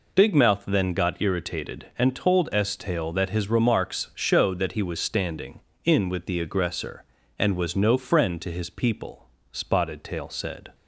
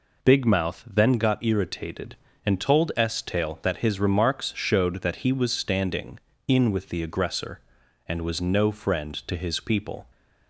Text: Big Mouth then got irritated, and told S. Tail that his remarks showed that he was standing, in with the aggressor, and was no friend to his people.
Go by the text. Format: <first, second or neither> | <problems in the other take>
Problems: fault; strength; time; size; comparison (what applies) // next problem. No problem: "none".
second | goes on to say "Spotted Tail said"; noticeable; from 9.5 s on; 1.2 s long